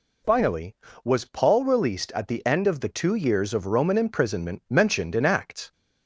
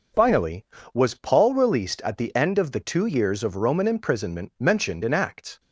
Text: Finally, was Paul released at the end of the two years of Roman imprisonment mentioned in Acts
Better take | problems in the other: first | gets quieter; strong; throughout; 7.5 dB

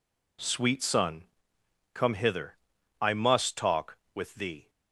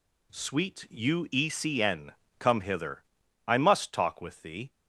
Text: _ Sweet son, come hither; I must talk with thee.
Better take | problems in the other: first | says "uecn" for "son"; at 0.9 s

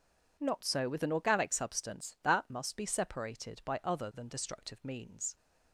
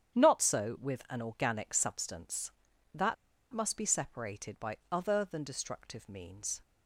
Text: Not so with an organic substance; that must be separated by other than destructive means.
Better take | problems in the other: first | starts louder than the rest; strong; until 1.2 s; 9.5 dB // pauses between "that" and "must"; at 3.1 s; 0.37 s long // pauses between "by" and "other"; slight; at 4.7 s; 0.16 s long

